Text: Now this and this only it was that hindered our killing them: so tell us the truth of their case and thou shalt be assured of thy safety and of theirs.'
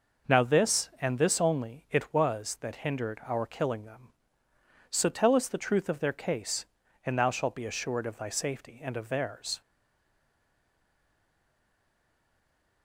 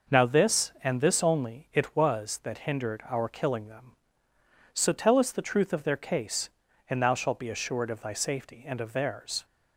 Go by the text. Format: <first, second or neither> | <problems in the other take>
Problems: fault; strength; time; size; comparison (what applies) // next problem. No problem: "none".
second | stays silent after the last word; strong; from 9.6 s on; 3.2 s long